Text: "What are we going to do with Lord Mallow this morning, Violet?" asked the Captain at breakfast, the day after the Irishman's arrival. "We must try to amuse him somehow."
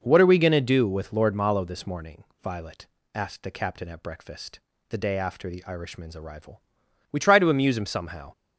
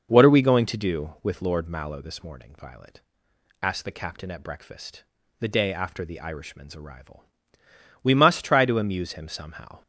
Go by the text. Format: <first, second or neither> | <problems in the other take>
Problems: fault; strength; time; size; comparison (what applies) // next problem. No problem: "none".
second | skips "must"; at 7.1 s